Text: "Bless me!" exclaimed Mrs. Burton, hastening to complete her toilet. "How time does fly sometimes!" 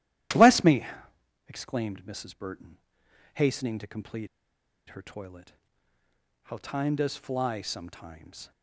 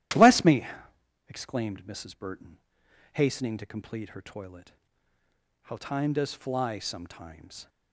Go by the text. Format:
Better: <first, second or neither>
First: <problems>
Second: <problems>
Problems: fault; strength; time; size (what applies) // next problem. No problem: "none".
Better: second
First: starts louder than the rest; strong; until 1.9 s; 13 dB // pauses between "complete" and "her"; noticeable; at 4.2 s; 0.61 s long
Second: starts louder than the rest; strong; until 1.7 s; 13 dB